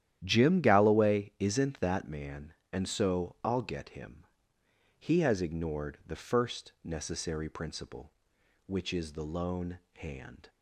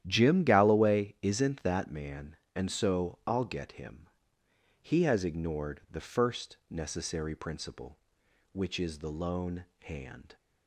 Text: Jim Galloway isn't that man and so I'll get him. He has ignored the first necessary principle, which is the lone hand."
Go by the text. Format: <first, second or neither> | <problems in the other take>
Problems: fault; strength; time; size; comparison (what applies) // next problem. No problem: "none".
neither | starts louder than the rest; strong; the same in both // pauses between "lone" and "hand"; slight; the same in both